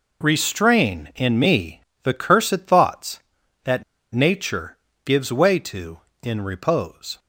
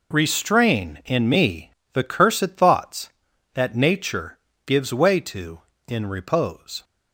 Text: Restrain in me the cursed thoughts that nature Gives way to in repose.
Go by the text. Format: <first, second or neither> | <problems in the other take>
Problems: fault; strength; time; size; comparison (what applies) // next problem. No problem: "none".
second | pauses between "me" and "the"; slight; at 1.8 s; 0.22 s long; slight in the second // pauses between "that" and "nature"; slight; at 3.8 s; 0.31 s long // pauses between "nature" and "Gives"; slight; at 4.7 s; 0.28 s long; slight in the second